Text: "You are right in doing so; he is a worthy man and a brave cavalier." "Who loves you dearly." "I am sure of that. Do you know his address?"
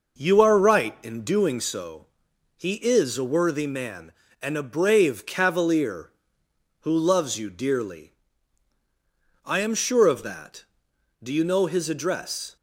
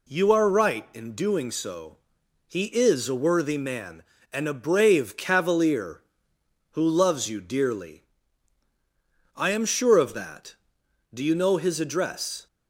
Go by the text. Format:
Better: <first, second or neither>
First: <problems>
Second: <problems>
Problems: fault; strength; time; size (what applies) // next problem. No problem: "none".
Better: second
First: starts louder than the rest; noticeable; until 1.9 s; 5.5 dB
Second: none